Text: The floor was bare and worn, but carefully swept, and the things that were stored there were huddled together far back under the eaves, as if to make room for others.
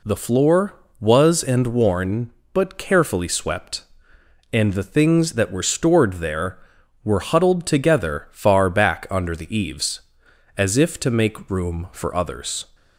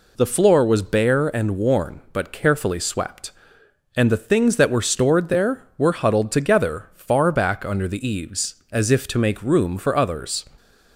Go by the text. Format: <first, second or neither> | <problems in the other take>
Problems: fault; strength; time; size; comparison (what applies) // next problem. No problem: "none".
second | skips "bare"; at 1.4 s